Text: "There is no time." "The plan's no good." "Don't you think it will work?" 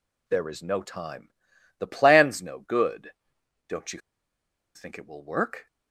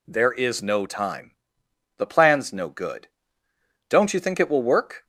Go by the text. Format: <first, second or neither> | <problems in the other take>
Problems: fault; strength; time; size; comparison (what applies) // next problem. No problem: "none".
second | pauses between "you" and "think"; noticeable; at 4.0 s; 0.74 s long